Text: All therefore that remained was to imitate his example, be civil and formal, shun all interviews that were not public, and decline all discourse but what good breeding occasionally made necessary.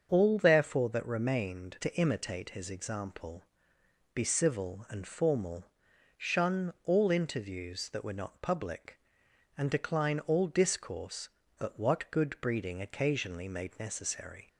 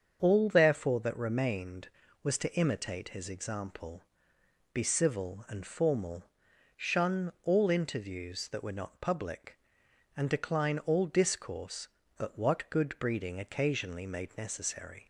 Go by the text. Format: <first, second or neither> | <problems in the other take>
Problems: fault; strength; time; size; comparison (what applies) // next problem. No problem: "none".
second | starts louder than the rest; until 1.1 s; 7 dB; strong in the second // skips "was"; at 1.7 s